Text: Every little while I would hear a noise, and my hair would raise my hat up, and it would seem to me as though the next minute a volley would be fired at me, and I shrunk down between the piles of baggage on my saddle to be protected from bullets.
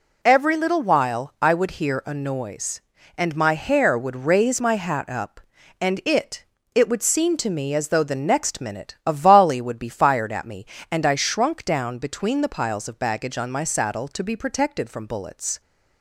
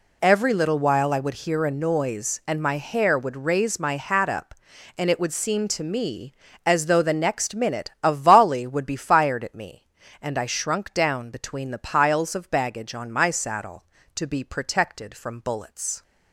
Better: second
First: says "it" twice; at 6.7 s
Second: none

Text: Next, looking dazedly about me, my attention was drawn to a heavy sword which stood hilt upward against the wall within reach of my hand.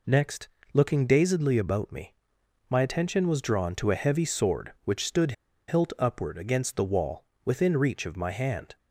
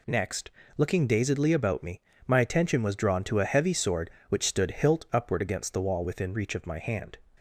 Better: second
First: pauses between "stood" and "hilt"; slight; at 5.3 s; 0.35 s long // pauses between "wall" and "within"; slight; at 7.2 s; 0.22 s long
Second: none

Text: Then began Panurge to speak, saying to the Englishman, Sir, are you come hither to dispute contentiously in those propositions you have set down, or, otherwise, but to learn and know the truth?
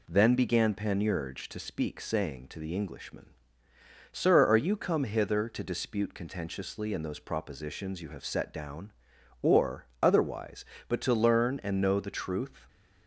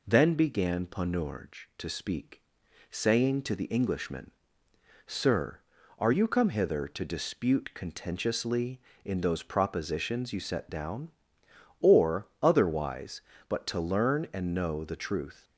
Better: first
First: none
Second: skips "have"; at 10.3 s

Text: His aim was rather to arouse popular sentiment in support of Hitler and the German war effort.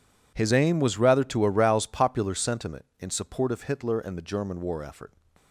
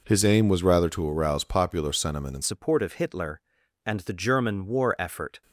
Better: first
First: none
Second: changes voice at "support"; from 2.4 s on; 3.0 s long

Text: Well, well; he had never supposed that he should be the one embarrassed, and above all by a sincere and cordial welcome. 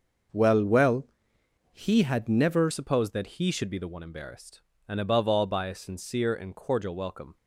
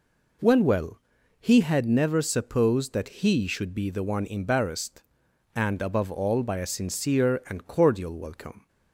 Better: second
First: starts louder than the rest; until 1.9 s; 6 dB // changes voice at "supposed"; from 2.7 s on; 4.6 s long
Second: none

